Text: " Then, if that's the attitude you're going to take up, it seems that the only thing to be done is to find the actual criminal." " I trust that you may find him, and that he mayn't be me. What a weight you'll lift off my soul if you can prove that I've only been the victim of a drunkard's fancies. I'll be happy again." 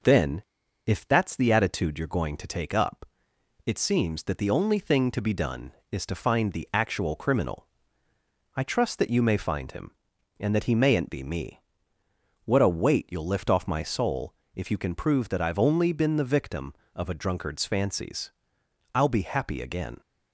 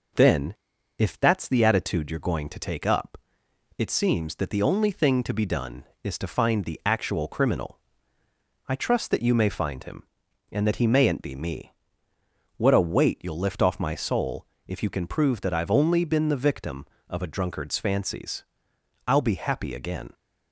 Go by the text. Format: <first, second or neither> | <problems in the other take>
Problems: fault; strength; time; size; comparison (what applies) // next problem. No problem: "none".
neither | pauses between "soul" and "if"; slight; the same in both